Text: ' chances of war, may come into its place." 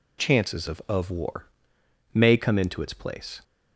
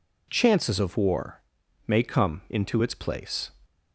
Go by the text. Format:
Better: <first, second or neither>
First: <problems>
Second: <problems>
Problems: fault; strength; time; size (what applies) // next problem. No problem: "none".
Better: second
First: says "of" twice; at 0.8 s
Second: none